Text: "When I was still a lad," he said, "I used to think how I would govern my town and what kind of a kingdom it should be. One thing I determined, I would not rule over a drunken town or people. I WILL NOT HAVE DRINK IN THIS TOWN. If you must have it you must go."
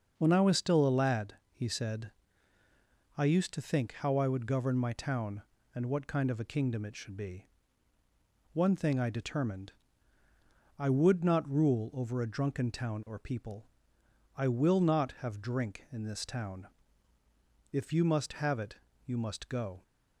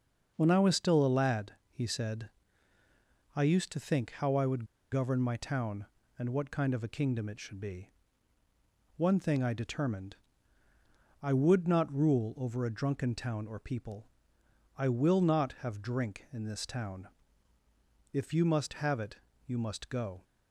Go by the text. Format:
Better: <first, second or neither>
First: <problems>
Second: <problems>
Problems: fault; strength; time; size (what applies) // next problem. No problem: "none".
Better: first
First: pauses between "it" and "you"; slight; at 18.7 s; 0.28 s long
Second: pauses between "would" and "govern"; slight; at 4.6 s; 0.28 s long // pauses between "it" and "you"; slight; at 19.1 s; 0.28 s long